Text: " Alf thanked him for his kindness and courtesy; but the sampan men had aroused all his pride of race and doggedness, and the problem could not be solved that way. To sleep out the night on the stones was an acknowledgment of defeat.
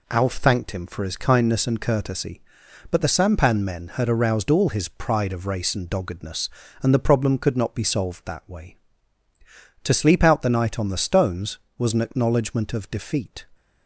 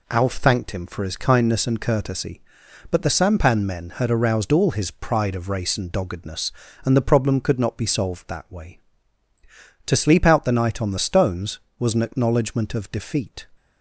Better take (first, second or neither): neither